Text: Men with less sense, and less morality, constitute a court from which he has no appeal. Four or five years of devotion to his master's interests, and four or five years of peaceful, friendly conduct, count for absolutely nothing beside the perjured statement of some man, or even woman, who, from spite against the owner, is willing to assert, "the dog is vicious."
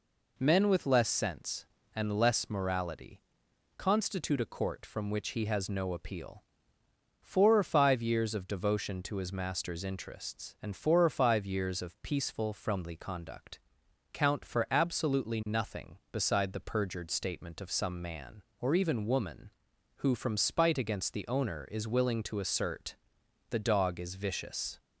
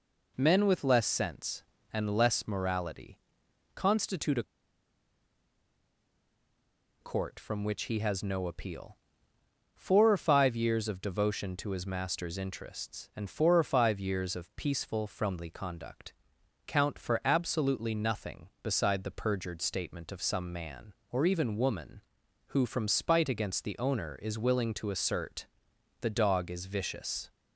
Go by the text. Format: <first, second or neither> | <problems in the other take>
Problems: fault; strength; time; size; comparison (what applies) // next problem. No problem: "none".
first | pauses between "a" and "court"; strong; at 4.4 s; 2.5 s long